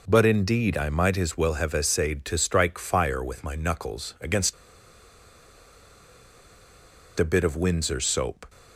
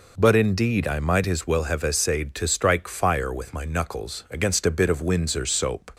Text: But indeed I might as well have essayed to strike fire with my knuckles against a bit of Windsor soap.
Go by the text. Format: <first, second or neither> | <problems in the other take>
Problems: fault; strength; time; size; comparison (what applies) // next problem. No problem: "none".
second | pauses between "against" and "a"; strong; at 4.5 s; 2.6 s long